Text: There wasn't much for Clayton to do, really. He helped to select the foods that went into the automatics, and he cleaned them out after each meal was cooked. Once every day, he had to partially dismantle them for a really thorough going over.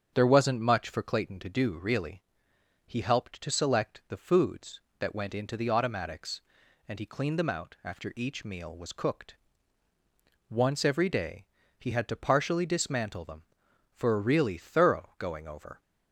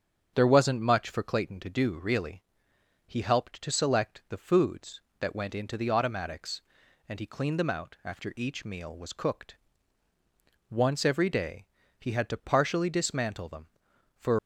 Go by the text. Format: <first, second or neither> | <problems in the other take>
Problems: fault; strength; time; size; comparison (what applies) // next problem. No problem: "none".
first | starts louder than the rest; strong; until 1.3 s; 7.5 dB; strong in the first // stops before "a really thorough going over"; at 14.3 s